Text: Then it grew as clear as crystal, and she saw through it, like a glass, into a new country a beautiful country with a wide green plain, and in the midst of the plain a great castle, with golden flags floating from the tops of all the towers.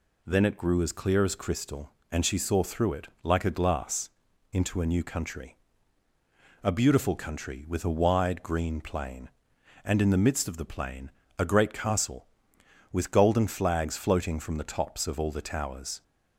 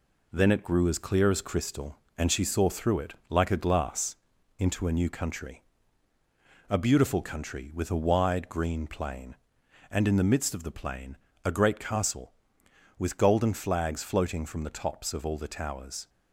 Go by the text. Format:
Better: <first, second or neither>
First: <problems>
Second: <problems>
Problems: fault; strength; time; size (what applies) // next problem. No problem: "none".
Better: first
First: pauses between "country" and "a"; at 5.5 s; 1.0 s long // pauses between "plain" and "a"; slight; at 11.0 s; 0.30 s long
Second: gets quieter; noticeable; throughout; 4.5 dB // pauses between "country" and "a"; at 5.6 s; 1.0 s long // pauses between "plain" and "a"; slight; at 11.1 s; 0.30 s long